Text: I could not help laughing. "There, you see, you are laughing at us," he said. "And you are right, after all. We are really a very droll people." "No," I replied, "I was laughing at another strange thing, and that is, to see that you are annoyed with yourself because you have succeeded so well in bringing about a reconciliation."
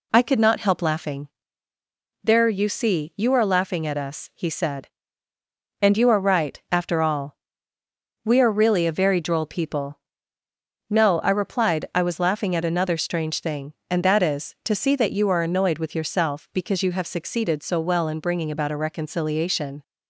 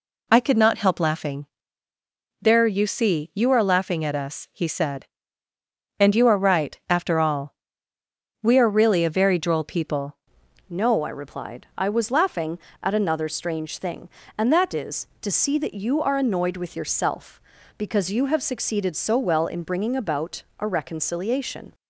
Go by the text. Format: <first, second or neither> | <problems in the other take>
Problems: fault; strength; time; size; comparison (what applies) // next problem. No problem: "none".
first | changes voice at "No"; from 10.6 s on; 11.1 s long // pauses between "about" and "a"; slight; at 20.4 s; 0.16 s long